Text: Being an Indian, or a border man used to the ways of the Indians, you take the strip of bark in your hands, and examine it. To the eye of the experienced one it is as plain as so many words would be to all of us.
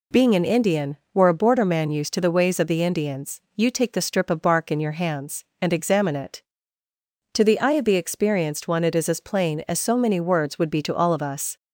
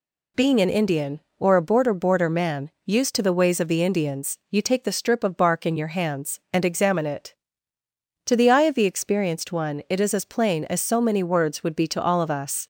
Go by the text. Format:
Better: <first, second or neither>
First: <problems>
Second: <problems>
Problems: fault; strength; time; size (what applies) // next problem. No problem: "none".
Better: first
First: none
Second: says "border" twice; at 1.9 s